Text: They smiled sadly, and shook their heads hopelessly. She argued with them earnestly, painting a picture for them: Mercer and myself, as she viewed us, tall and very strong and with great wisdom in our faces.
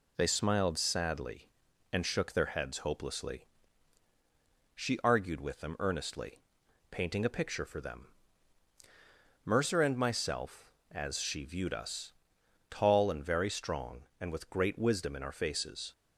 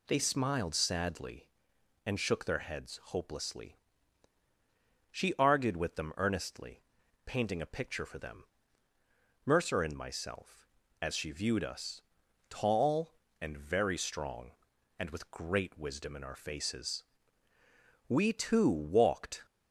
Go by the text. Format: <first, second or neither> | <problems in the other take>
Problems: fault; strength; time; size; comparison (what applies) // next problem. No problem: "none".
first | goes on to say "We too walked"; from 18.0 s on; 1.3 s long